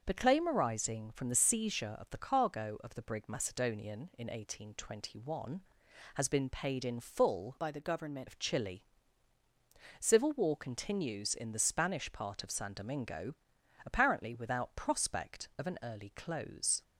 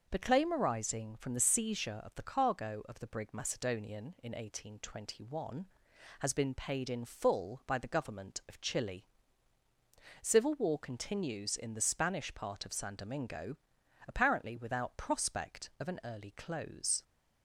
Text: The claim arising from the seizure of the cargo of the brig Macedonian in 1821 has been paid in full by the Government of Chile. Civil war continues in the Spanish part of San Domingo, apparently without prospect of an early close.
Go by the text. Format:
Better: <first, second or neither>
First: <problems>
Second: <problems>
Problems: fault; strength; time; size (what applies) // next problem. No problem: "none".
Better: second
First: starts louder than the rest; until 1.0 s; 6.5 dB // changes voice from "by" to "Government"; from 7.5 to 8.2 s; 0.7 s long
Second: none